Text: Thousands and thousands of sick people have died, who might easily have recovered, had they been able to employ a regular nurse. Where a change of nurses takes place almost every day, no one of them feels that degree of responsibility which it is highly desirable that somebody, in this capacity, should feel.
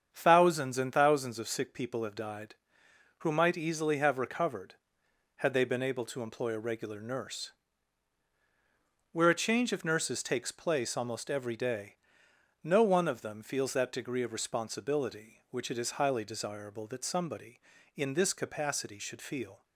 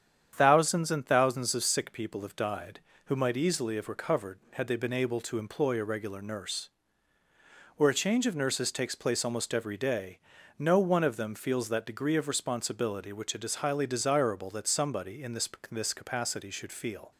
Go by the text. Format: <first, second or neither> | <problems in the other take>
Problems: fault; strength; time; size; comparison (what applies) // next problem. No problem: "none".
first | starts louder than the rest; strong; until 1.3 s; 8.5 dB; strong in the first // says "this" twice; at 15.7 s